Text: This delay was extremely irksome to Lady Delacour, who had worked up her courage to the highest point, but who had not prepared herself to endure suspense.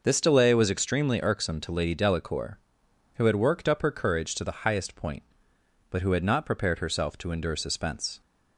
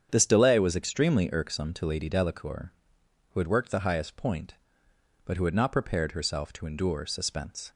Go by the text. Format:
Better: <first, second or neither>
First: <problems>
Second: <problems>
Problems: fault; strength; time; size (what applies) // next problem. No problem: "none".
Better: first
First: none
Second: starts louder than the rest; strong; until 1.1 s; 8 dB // skips "up her courage to"; at 3.7 s